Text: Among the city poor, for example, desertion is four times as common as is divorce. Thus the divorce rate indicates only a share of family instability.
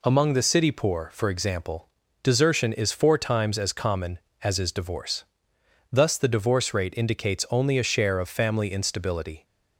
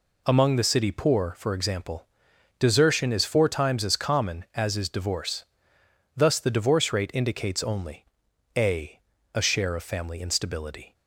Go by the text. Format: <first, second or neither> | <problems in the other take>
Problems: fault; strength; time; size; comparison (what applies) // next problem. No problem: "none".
first | pauses between "only" and "a"; noticeable; at 8.0 s; 0.50 s long // says "a" twice; at 9.3 s